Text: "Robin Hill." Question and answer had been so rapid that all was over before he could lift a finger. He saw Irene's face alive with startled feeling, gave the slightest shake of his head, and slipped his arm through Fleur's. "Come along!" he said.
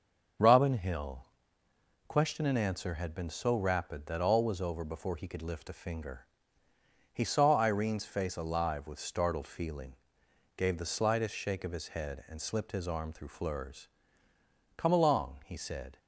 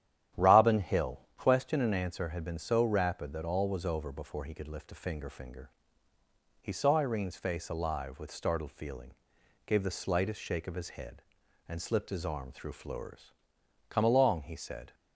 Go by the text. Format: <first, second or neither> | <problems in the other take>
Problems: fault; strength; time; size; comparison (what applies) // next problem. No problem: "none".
first | starts louder than the rest; strong; until 1.5 s; 11 dB; also in the first // says "finger" twice; at 5.2 s